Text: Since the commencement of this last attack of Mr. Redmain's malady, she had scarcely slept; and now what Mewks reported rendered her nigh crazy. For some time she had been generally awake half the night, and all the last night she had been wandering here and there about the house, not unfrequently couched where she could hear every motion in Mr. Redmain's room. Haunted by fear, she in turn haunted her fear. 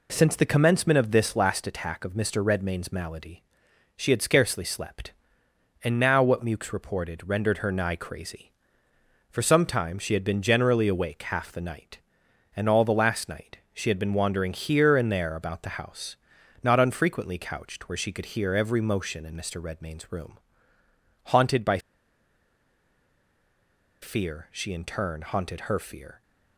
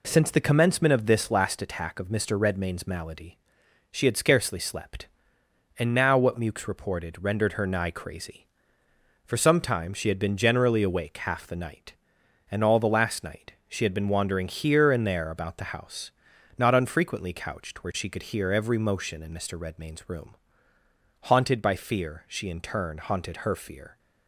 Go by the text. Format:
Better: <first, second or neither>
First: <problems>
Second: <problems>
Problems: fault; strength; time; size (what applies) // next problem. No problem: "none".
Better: second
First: pauses between "by" and "fear"; strong; at 21.7 s; 2.2 s long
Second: none